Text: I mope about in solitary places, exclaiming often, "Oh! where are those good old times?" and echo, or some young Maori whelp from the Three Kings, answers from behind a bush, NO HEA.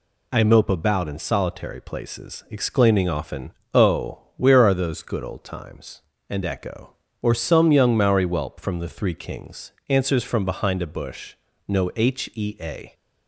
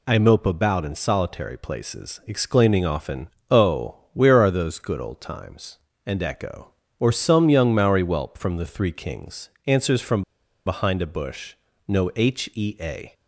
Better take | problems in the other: first | pauses between "from" and "behind"; at 10.2 s; 0.43 s long

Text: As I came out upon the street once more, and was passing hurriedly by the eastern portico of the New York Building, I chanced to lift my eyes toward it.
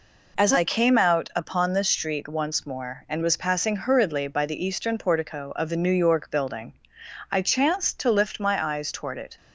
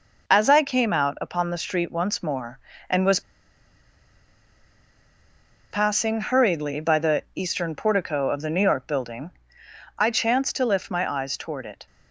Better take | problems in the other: first | pauses between "was" and "passing"; strong; at 3.1 s; 2.5 s long

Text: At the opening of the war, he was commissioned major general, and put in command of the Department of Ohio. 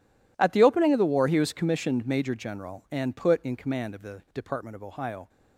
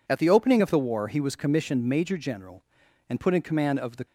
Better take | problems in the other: first | stops before "Department of Ohio"; at 4.0 s

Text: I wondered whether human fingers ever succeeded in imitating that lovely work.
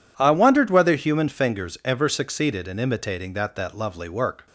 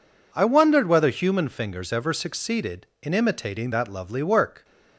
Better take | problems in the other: second | says "that" twice; at 3.5 s

